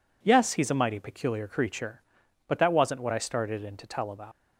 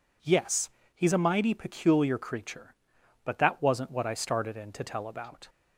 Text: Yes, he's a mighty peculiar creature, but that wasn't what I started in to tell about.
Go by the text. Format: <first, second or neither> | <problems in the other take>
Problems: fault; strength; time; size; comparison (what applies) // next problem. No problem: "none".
second | leaves "about" unfinished; at 4.3 s; 95 ms